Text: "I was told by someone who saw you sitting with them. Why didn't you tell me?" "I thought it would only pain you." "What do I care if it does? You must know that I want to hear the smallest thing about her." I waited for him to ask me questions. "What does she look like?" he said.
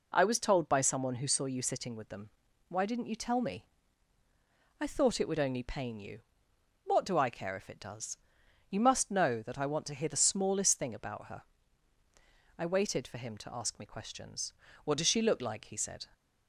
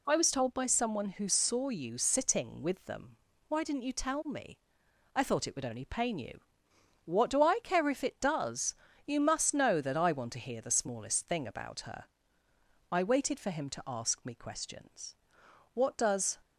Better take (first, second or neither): first